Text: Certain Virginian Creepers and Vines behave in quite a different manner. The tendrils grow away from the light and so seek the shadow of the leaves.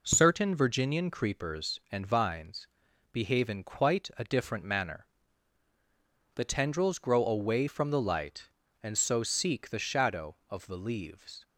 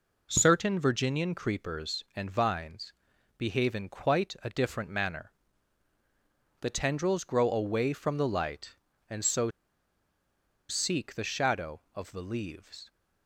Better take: first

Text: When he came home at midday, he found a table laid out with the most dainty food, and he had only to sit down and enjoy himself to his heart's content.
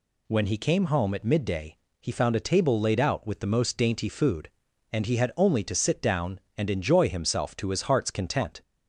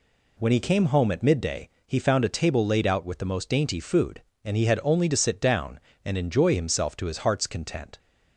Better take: neither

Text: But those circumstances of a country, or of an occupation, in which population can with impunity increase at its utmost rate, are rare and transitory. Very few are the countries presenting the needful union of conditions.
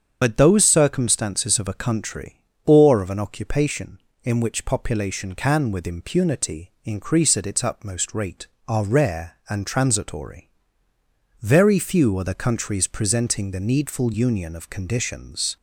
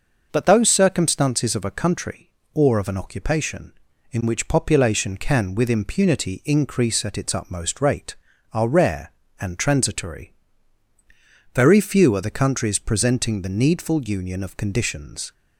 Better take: second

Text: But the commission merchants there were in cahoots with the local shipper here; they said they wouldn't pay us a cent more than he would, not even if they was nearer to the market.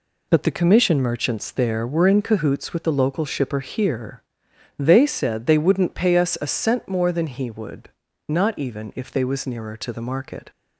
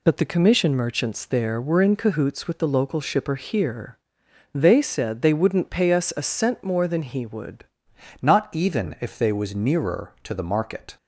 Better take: first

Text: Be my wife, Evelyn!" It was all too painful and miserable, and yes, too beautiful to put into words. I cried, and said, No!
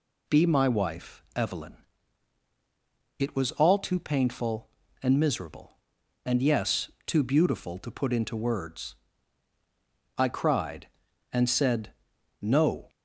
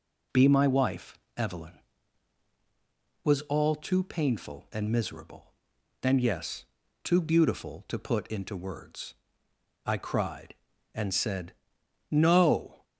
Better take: first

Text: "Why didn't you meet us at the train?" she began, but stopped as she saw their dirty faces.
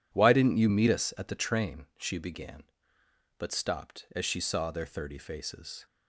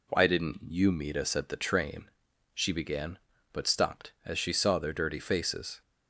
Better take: second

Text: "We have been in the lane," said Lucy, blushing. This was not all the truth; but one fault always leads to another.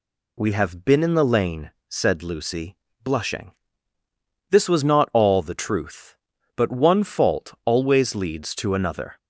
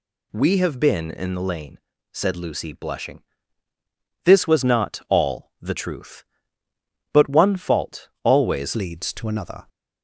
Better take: first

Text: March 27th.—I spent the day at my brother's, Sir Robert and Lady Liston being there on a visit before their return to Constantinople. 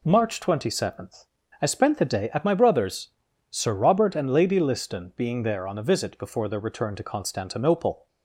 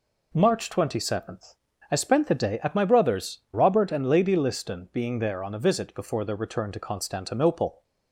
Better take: first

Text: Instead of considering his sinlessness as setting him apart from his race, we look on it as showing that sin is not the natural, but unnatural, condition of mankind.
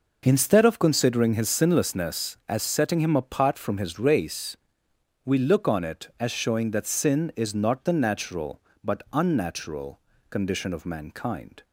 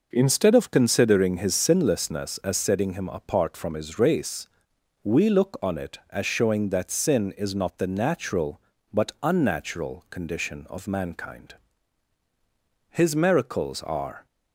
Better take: first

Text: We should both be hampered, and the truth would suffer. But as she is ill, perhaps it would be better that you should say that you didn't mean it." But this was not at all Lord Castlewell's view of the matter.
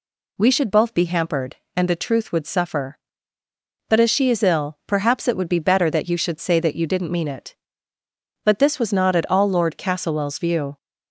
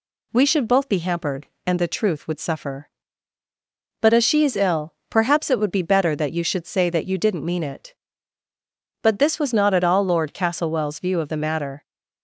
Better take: second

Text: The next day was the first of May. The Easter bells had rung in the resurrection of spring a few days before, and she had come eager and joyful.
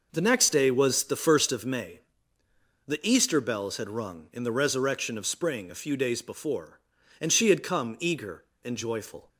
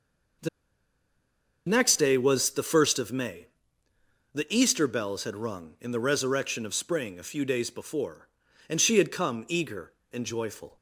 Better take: first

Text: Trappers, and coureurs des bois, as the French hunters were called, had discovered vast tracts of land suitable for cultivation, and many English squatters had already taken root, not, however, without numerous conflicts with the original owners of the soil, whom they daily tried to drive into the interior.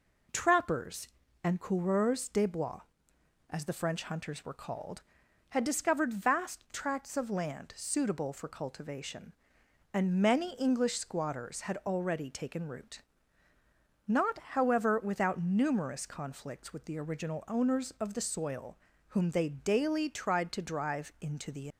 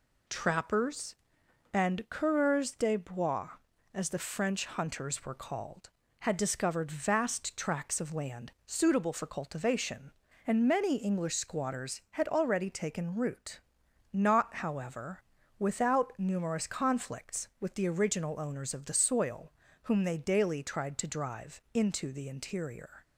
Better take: second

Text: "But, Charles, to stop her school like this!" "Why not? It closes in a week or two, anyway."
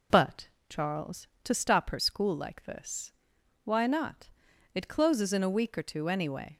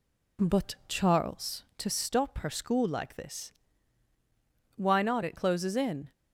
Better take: first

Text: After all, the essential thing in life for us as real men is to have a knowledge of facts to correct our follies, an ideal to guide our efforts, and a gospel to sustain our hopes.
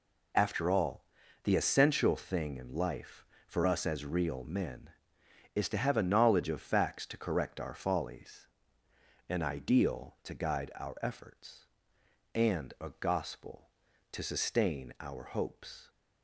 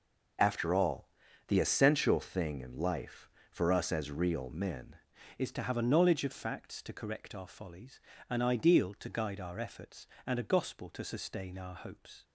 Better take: first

